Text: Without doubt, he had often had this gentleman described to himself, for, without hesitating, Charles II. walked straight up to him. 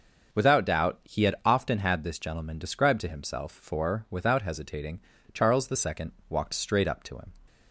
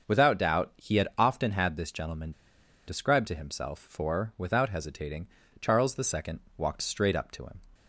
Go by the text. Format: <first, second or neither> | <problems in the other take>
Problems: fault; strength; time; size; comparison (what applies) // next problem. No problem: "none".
first | pauses between "gentleman" and "described"; noticeable; at 2.3 s; 0.55 s long